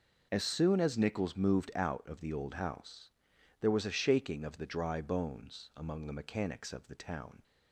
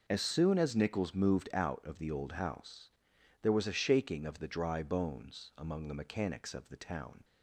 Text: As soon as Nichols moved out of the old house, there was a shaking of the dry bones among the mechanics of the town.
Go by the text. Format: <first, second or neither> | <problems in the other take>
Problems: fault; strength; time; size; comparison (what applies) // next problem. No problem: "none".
neither | none